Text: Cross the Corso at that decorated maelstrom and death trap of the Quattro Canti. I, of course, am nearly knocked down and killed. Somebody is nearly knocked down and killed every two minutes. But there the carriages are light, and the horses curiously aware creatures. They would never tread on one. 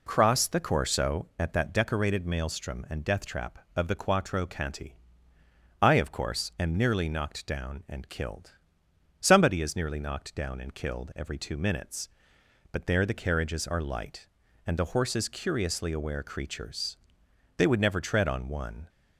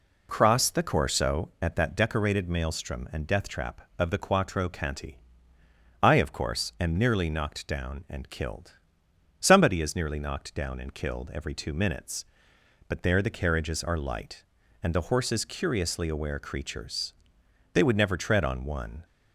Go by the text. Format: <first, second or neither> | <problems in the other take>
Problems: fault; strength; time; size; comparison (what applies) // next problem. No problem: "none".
neither | none